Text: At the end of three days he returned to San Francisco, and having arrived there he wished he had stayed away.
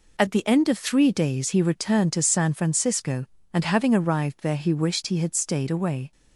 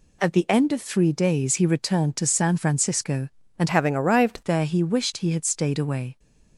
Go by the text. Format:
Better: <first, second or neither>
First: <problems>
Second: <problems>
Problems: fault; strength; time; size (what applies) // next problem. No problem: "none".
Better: first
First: none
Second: changes voice from "having" to "arrived"; from 3.6 to 4.4 s; 0.8 s long